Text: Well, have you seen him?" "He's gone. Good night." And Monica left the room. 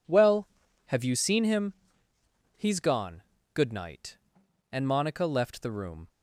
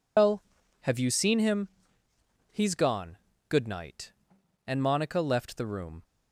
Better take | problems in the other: first | loses the start of "Well"; at 0.1 s; 155 ms

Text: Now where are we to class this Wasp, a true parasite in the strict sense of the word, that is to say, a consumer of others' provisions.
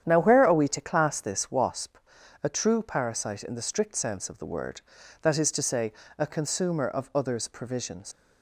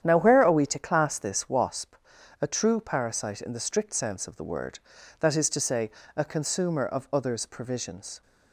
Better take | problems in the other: second | starts louder than the rest; strong; until 1.0 s; 9 dB; strong in the second // leaves "provisions" unfinished; at 8.1 s; 120 ms

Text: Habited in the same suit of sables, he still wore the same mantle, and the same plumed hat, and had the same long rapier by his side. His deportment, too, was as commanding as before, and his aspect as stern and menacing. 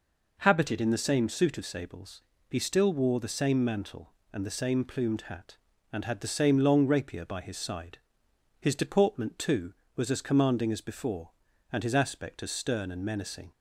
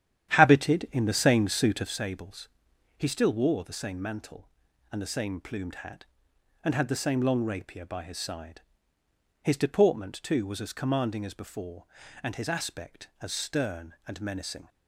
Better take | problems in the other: first | starts louder than the rest; strong; until 2.0 s; 10.5 dB

